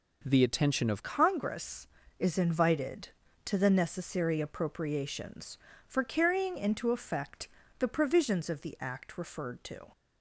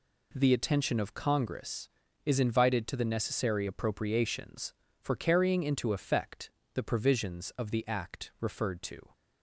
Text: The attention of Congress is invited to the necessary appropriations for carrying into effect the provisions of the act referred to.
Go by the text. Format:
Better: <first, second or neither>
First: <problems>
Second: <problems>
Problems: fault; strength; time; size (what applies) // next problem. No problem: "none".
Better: second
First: changes voice at "Congress"; from 1.0 s on; 8.9 s long // pauses between "effect" and "the"; slight; at 7.4 s; 0.30 s long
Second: pauses between "effect" and "the"; slight; at 6.5 s; 0.24 s long